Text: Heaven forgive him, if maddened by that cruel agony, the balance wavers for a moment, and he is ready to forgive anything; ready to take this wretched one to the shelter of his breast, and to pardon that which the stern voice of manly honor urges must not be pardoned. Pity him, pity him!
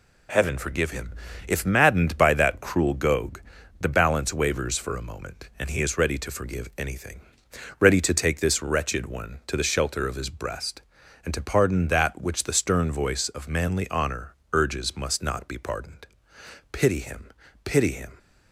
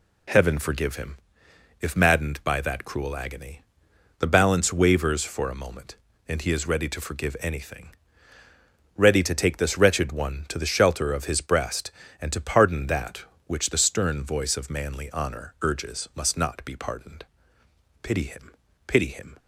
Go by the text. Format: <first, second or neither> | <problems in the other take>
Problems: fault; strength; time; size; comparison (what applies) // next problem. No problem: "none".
second | says "gogue" for "agony"; at 2.9 s // pauses between "honor" and "urges"; slight; at 14.3 s; 0.16 s long